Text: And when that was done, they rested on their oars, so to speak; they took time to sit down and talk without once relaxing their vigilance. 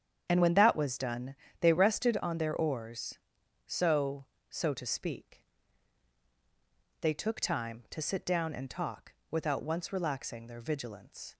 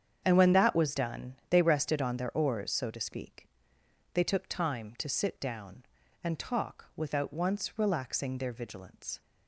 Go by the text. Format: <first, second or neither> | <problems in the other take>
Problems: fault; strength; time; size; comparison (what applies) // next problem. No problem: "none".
second | starts louder than the rest; strong; until 1.3 s; 8.5 dB; strong in the second // says "so" twice; at 4.4 s // pauses between "talk" and "without"; slight; at 9.1 s; 0.18 s long